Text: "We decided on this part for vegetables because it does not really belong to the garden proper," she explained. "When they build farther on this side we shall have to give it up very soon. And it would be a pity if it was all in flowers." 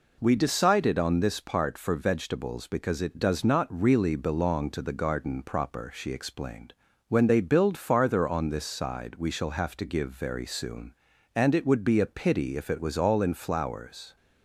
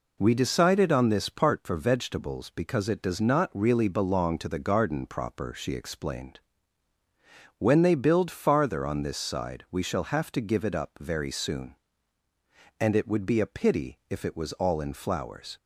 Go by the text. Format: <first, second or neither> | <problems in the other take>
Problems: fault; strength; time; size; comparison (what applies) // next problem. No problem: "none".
second | skips "it up"; at 10.0 s